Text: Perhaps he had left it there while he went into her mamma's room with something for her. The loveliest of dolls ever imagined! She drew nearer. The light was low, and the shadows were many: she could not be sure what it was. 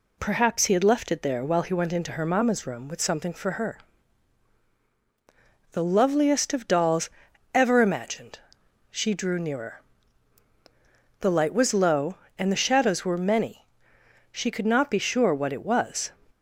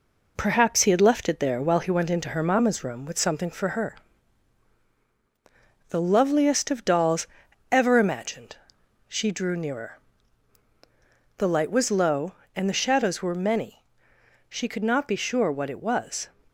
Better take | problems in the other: first | gets quieter; throughout; 3.5 dB // pauses between "dolls" and "ever"; noticeable; at 7.2 s; 0.46 s long; noticeable in the first

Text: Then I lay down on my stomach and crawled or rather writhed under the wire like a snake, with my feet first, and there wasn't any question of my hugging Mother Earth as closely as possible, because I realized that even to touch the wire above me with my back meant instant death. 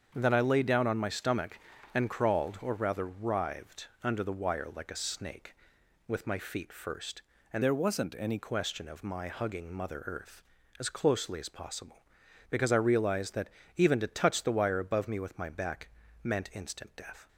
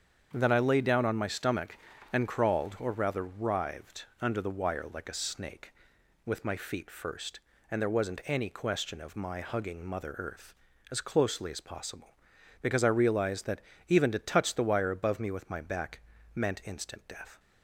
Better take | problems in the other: second | starts louder than the rest; strong; until 1.1 s; 7.5 dB; strong in the second // changes voice from "there" to "any"; from 7.6 to 8.3 s; 0.7 s long // pauses between "that" and "even"; slight; at 13.4 s; 0.26 s long; slight in the second // pauses between "back" and "meant"; slight; at 15.8 s; 0.36 s long; slight in the second

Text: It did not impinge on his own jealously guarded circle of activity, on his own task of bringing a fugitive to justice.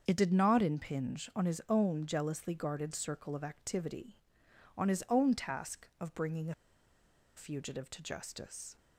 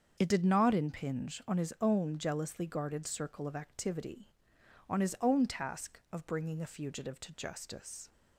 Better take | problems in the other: second | starts louder than the rest; until 1.0 s; 7 dB; also in the second // pauses between "a" and "fugitive"; noticeable; at 6.5 s; 0.82 s long

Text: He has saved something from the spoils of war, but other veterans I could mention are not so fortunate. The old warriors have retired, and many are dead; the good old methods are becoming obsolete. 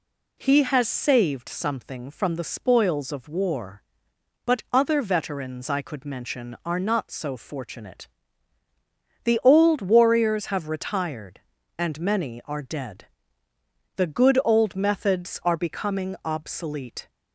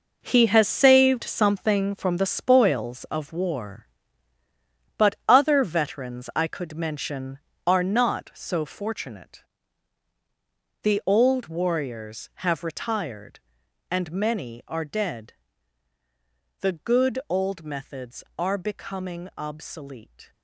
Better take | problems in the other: first | gets quieter; strong; throughout; 10.5 dB

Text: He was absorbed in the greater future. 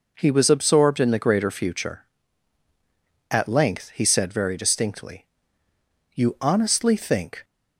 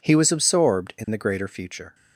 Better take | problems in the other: second | goes on to say "At length he said very distinctly You honestly think"; strong; from 3.2 s on; 4.1 s long

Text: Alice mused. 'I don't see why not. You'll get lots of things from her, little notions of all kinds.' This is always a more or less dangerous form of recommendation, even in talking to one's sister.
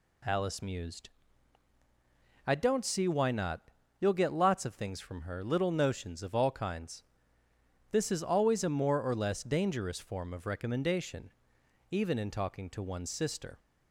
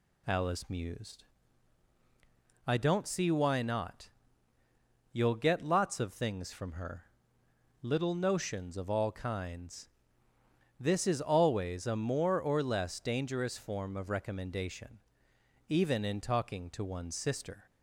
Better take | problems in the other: neither | none

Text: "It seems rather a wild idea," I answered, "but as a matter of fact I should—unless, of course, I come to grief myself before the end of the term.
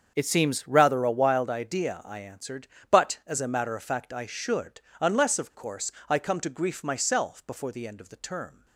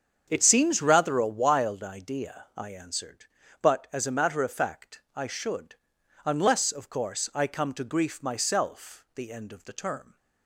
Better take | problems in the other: first | starts louder than the rest; strong; until 1.2 s; 7.5 dB; also in the first // skips "before"; at 9.0 s

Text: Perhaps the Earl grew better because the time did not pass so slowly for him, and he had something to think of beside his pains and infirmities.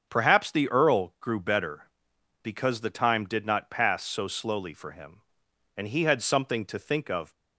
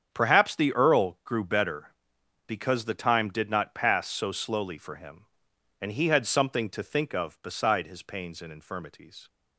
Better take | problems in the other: second | starts louder than the rest; until 1.1 s; 7 dB; strong in the second // stops before "beside his pains and infirmities"; at 7.3 s

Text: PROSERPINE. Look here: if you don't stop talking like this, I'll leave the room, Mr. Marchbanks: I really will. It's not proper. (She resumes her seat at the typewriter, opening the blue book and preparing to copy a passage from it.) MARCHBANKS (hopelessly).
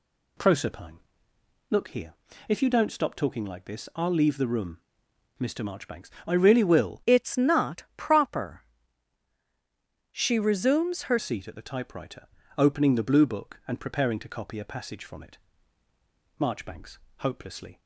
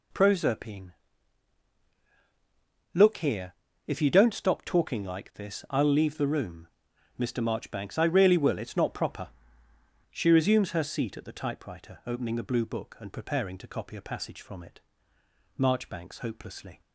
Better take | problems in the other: second | changes voice from "It's" to "her"; from 7.0 to 11.1 s; 4.1 s long

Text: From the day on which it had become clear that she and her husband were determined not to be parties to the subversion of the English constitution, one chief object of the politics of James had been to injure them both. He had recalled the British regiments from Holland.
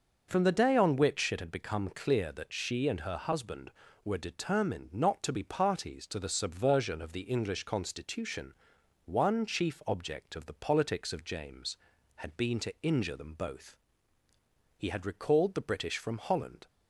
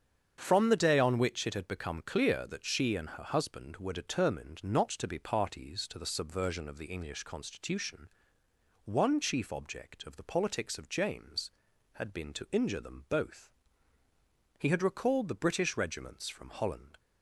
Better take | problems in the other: second | starts louder than the rest; until 1.3 s; 6.5 dB; strong in the second // skips "regiments"; at 15.9 s

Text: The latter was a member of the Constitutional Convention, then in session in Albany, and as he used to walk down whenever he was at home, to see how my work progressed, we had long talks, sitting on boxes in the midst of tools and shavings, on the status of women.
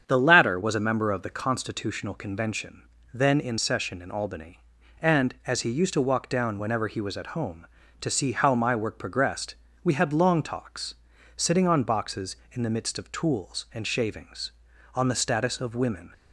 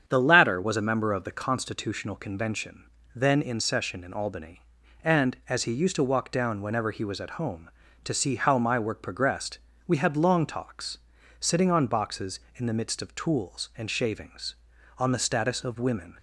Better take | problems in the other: neither | starts louder than the rest; strong; the same in both

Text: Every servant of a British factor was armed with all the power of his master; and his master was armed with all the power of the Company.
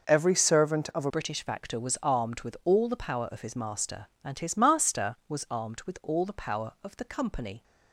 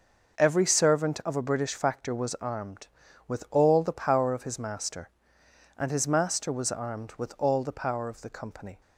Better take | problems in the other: second | changes voice at "British"; from 1.0 s on; 6.6 s long

